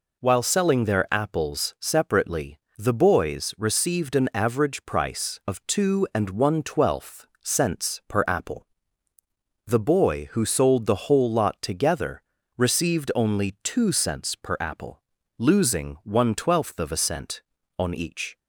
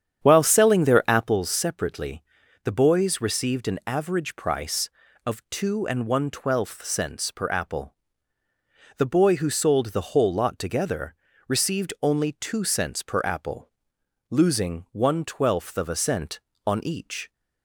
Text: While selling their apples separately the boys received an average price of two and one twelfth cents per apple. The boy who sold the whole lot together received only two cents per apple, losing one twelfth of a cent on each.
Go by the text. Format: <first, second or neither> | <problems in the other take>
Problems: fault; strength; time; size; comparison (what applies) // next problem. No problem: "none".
first | starts louder than the rest; strong; until 1.4 s; 8.5 dB // pauses between "separately" and "the"; at 2.2 s; 0.40 s long; slight in the first // pauses between "together" and "received"; slight; at 11.1 s; 0.34 s long; slight in the first